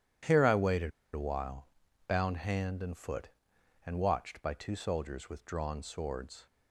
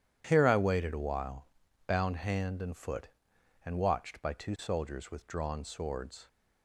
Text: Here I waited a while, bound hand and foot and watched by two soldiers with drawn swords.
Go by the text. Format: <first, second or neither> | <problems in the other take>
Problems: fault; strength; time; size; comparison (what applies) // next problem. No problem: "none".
second | pauses between "waited" and "a"; slight; at 0.8 s; 0.23 s long